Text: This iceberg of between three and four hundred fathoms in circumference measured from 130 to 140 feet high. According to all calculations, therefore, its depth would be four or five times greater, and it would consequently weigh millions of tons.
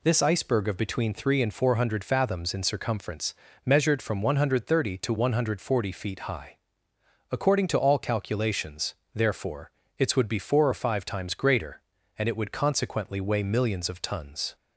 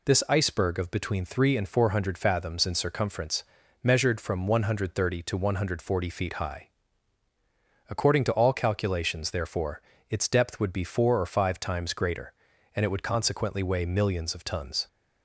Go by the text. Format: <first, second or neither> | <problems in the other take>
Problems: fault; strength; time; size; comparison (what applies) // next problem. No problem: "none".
second | pauses between "circumference" and "measured"; slight; at 3.3 s; 0.32 s long; also in the second // skips "depth"; at 10.1 s